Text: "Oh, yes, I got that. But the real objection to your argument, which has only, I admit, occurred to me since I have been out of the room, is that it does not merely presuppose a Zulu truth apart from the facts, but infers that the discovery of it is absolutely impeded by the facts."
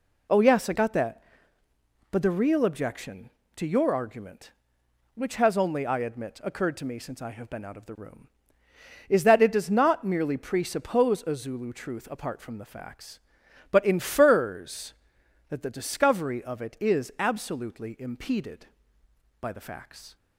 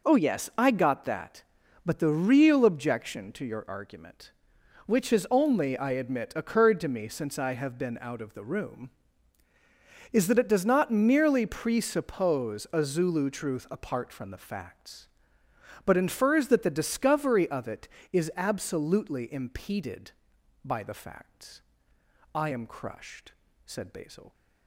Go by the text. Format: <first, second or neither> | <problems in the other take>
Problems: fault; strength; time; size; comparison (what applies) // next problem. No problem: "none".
first | goes on to say "I am crushed said Basil"; strong; from 22.3 s on; 1.9 s long